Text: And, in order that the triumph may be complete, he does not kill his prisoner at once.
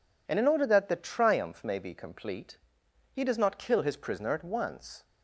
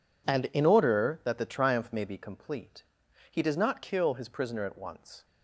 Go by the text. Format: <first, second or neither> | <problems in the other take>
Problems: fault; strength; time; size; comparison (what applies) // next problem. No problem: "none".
neither | none